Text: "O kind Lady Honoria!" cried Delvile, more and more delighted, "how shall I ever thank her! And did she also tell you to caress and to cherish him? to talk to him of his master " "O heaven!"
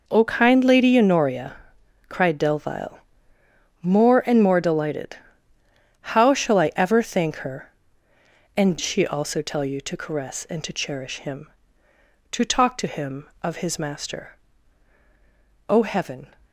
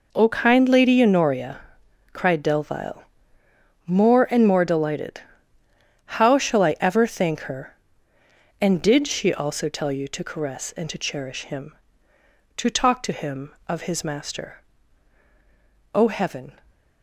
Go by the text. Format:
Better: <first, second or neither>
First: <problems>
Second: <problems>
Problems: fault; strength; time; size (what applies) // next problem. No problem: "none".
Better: second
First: skips "did"; at 8.7 s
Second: none